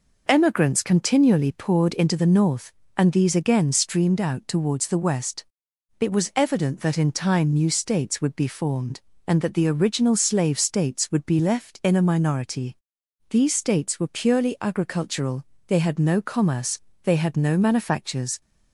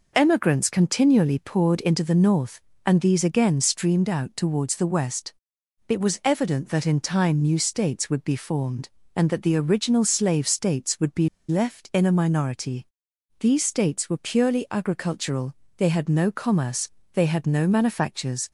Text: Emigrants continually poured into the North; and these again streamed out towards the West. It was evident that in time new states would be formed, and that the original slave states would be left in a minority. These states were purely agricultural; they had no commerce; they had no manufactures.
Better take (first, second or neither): first